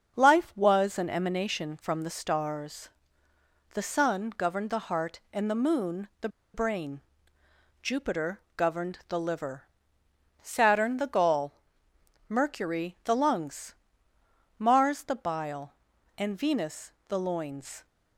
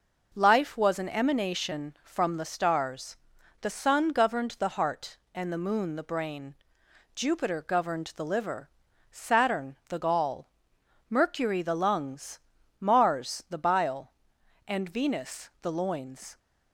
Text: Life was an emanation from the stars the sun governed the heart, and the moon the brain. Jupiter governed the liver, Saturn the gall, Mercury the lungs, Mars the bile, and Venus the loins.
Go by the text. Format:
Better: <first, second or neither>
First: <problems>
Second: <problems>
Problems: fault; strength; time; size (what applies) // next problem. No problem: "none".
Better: second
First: starts louder than the rest; until 1.2 s; 6.5 dB // pauses between "stars" and "the"; noticeable; at 2.8 s; 0.84 s long // pauses between "the" and "brain"; slight; at 6.2 s; 0.26 s long // pauses between "Jupiter" and "governed"; slight; at 8.4 s; 0.16 s long // pauses between "Venus" and "the"; slight; at 16.9 s; 0.16 s long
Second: pauses between "stars" and "the"; at 3.1 s; 0.44 s long